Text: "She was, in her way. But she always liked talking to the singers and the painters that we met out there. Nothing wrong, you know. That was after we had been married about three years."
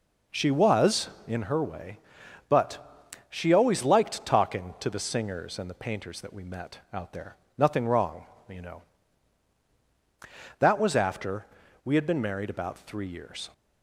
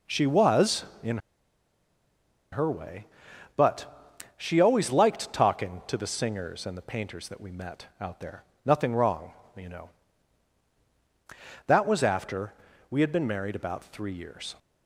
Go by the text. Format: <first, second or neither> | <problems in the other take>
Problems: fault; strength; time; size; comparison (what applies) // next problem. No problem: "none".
first | pauses between "in" and "her"; strong; at 1.1 s; 1.3 s long // pauses between "But" and "she"; slight; at 4.1 s; 0.18 s long; slight in the first // pauses between "after" and "we"; at 12.5 s; 0.38 s long; also in the first